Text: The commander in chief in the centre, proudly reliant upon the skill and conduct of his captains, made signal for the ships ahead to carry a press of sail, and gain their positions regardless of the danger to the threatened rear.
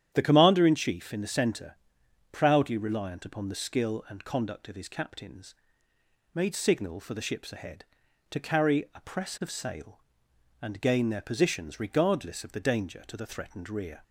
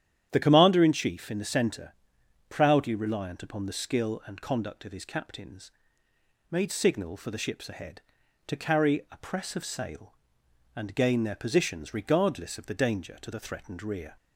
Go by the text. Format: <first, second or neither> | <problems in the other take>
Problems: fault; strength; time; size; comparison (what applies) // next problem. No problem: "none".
neither | starts louder than the rest; strong; the same in both